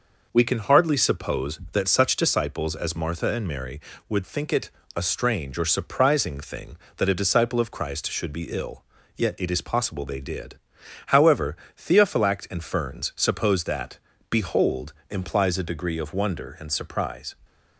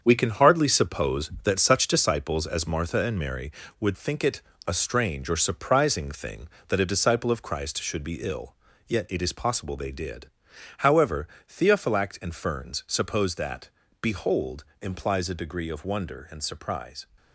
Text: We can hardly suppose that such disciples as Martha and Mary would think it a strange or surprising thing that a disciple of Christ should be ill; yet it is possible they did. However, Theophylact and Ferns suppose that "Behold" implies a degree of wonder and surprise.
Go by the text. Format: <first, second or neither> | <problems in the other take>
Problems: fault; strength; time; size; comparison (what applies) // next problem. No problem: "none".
first | gets quieter; strong; throughout; 8 dB // pauses between "it" and "a"; slight; at 4.4 s; 0.26 s long; slight in the first // pauses between "that" and "Behold"; slight; at 13.6 s; 0.32 s long; slight in the first // pauses between "Behold" and "implies"; slight; at 14.6 s; 0.16 s long; slight in the first